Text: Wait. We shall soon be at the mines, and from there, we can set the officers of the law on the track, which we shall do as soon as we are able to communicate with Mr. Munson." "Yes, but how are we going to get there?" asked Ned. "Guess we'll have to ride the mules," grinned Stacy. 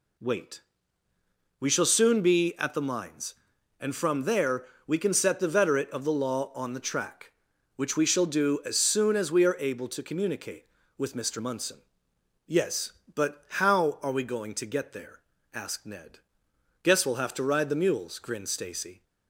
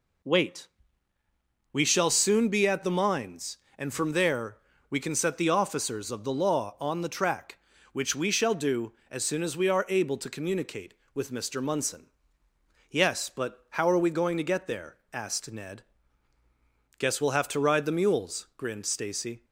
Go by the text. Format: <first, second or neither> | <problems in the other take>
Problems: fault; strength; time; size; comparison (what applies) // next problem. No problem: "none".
second | says "veterate" for "officers"; at 5.4 s